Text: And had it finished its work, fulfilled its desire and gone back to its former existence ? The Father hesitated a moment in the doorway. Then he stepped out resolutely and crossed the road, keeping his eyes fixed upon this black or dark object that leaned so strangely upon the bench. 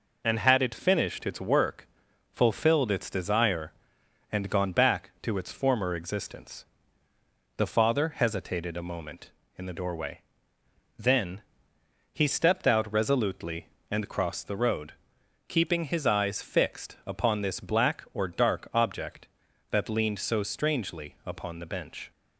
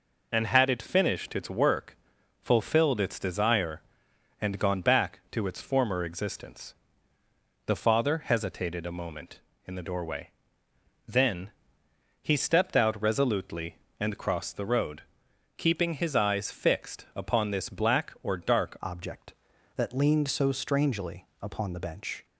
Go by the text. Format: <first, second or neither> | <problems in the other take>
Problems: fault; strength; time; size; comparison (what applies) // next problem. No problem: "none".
first | pauses between "Then" and "he"; noticeable; at 11.4 s; 0.72 s long; noticeable in the first // changes voice at "object"; from 18.8 s on; 3.4 s long // pauses between "strangely" and "upon"; slight; at 21.2 s; 0.16 s long